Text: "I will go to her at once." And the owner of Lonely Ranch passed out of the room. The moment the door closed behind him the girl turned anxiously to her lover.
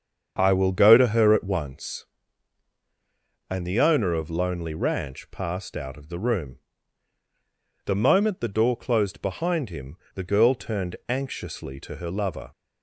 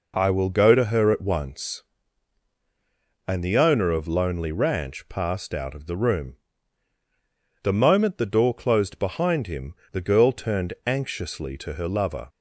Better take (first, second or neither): second